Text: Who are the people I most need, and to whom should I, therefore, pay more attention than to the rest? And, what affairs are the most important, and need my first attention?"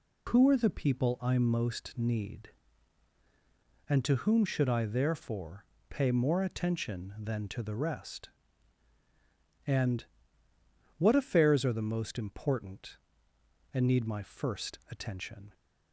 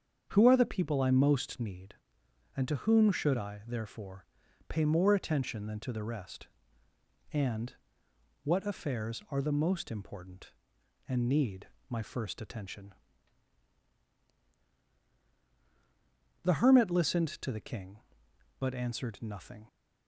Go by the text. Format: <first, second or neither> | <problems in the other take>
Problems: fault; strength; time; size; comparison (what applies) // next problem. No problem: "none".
first | starts louder than the rest; strong; until 1.2 s; 7.5 dB // pauses between "need" and "my"; slight; at 11.6 s; 0.22 s long // goes on to say "The hermit listened to the King but answered nothing"; strong; from 16.4 s on; 3.2 s long